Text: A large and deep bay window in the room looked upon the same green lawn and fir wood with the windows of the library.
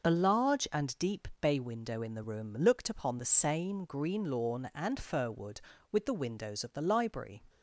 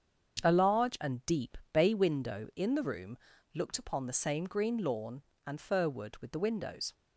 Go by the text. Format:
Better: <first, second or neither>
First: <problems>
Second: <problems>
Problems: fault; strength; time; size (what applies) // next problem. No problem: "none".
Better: first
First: starts louder than the rest; noticeable; until 1.1 s; 6 dB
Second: starts louder than the rest; strong; until 1.4 s; 7.5 dB // pauses between "deep" and "bay"; slight; at 1.5 s; 0.16 s long // pauses between "room" and "looked"; slight; at 3.1 s; 0.36 s long // stops before "of the library"; at 6.9 s